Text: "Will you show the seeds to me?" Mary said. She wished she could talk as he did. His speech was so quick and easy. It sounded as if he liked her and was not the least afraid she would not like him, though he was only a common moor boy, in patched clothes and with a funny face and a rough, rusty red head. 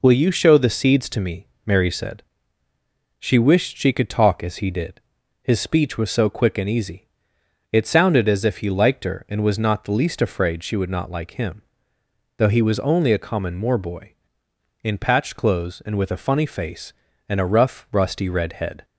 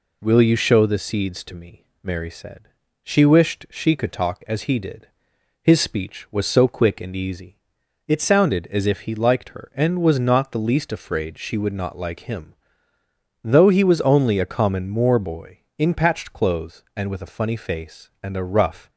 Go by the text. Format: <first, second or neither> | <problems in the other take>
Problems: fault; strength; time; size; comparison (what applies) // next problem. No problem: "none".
first | stops before "rusty red head"; at 18.8 s